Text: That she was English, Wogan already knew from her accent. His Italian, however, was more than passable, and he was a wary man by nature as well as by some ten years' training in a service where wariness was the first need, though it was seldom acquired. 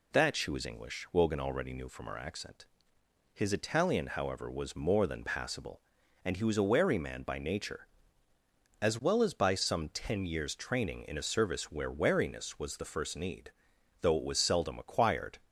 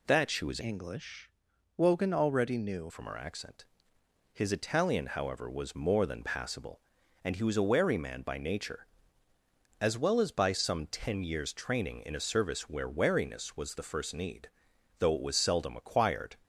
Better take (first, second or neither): first